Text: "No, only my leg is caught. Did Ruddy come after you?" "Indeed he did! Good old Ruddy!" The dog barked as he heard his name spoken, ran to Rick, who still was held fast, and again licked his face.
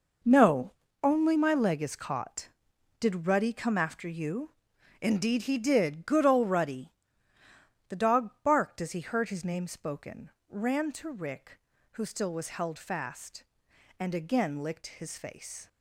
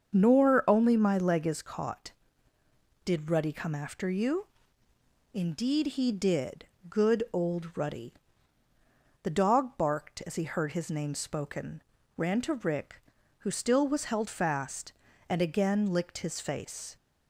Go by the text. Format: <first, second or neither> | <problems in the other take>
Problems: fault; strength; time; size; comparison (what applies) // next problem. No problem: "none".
first | starts louder than the rest; until 1.2 s; 6.5 dB // says "Nor" for "No"; at 0.1 s